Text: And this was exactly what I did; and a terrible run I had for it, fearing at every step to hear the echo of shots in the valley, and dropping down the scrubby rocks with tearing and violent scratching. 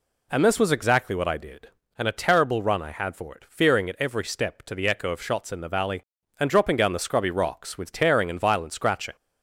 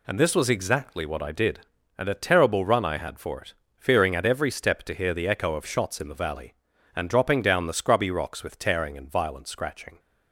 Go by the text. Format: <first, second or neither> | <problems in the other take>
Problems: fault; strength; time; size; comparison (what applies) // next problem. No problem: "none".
second | skips "hear"; at 4.7 s